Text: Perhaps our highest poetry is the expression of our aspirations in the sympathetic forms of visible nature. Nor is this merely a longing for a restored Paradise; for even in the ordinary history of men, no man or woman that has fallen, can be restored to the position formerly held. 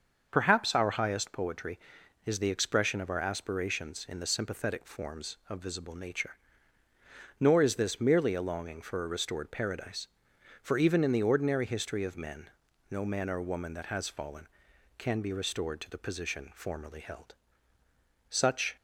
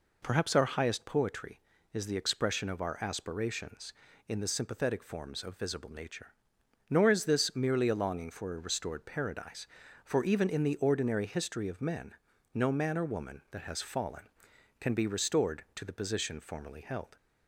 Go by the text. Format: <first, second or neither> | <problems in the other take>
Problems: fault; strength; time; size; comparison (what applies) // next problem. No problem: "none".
second | starts louder than the rest; until 1.3 s; 6.5 dB // goes on to say "Such"; slight; from 18.2 s on; 0.48 s long